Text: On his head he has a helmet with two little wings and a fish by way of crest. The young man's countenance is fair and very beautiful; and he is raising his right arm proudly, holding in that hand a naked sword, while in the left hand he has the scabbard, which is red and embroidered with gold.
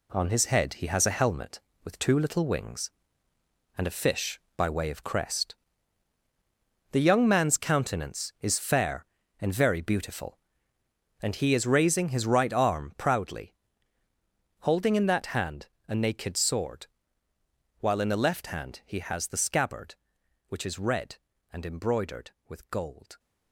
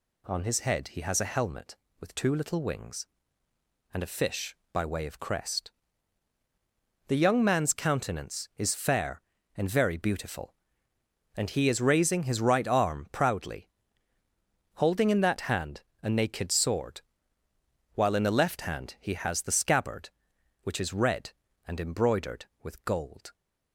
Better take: second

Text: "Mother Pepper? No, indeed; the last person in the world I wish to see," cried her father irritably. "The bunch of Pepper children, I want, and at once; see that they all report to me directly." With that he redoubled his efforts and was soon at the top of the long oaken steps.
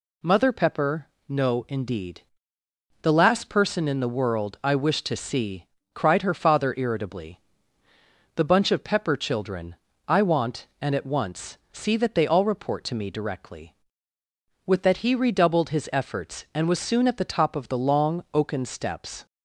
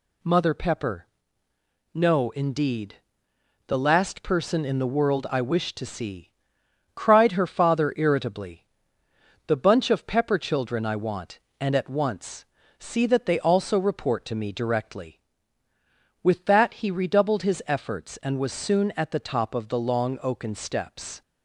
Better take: first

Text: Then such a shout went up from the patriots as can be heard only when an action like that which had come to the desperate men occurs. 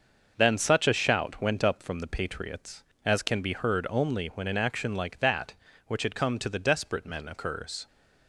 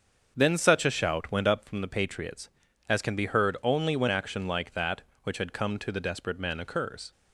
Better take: first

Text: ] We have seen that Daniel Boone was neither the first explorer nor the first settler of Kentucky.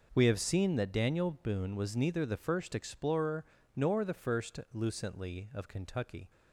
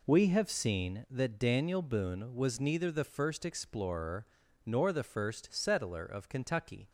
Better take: second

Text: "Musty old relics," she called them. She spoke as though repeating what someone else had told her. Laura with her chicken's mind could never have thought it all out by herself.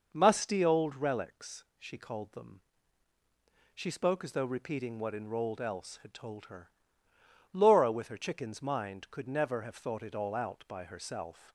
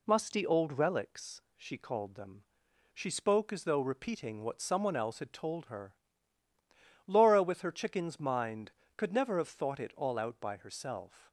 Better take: second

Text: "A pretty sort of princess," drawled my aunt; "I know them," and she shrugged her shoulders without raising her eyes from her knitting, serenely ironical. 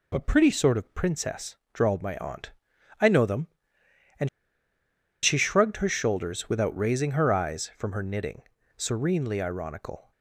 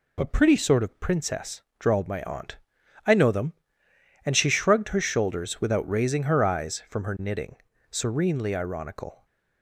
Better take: second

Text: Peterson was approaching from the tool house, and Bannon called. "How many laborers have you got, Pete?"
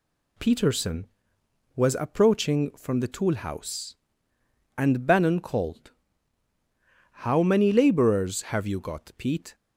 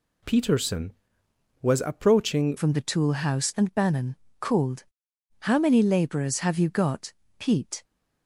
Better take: first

